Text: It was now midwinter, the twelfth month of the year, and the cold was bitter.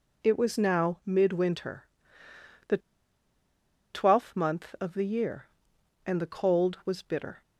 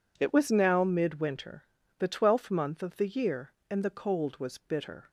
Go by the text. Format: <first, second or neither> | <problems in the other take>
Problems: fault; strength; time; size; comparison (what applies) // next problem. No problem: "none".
second | pauses between "the" and "twelfth"; at 2.7 s; 1.1 s long